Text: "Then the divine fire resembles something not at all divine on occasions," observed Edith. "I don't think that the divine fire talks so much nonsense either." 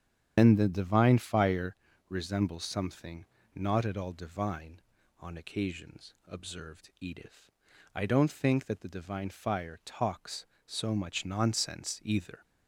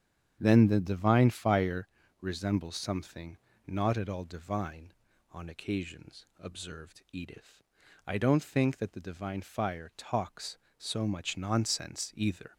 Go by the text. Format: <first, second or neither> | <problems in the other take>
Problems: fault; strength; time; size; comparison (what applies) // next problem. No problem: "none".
second | loses the start of "Then"; at 0.3 s; 90 ms // starts louder than the rest; strong; until 1.3 s; 8 dB; strong in the second // pauses between "fire" and "resembles"; slight; at 1.7 s; 0.32 s long; slight in the second // pauses between "something" and "not"; slight; at 3.2 s; 0.30 s long; slight in the second